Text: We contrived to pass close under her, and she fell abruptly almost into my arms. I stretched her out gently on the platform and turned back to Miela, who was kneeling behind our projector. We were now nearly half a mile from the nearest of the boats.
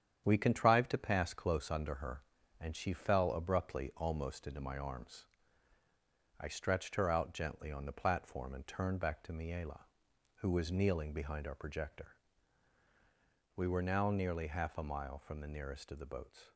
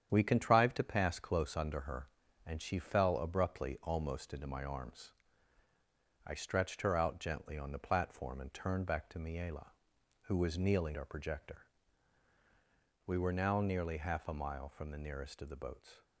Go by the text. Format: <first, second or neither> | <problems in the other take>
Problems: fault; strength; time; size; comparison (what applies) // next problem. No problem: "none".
first | starts louder than the rest; strong; until 1.1 s; 9 dB; strong in the first // skips "behind"; at 10.9 s